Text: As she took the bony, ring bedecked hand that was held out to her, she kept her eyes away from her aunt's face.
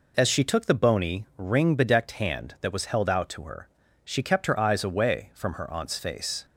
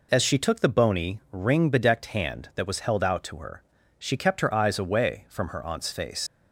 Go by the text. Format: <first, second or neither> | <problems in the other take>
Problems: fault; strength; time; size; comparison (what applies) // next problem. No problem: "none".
first | leaves "face" unfinished; at 6.2 s; 115 ms